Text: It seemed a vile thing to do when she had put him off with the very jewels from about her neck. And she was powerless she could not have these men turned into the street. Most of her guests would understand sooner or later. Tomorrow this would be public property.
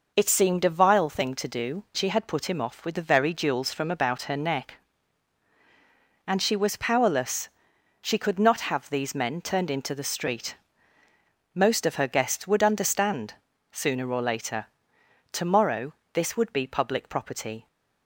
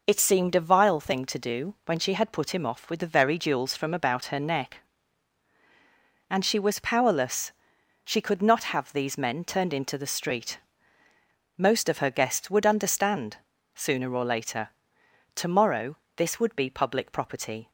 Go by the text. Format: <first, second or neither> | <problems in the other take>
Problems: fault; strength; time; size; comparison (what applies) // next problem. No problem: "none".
second | skips "when"; at 1.8 s // pauses between "powerless" and "she"; noticeable; at 7.4 s; 0.52 s long; noticeable in the second // pauses between "understand" and "sooner"; at 13.3 s; 0.40 s long; also in the second // pauses between "Tomorrow" and "this"; slight; at 15.9 s; 0.20 s long; slight in the second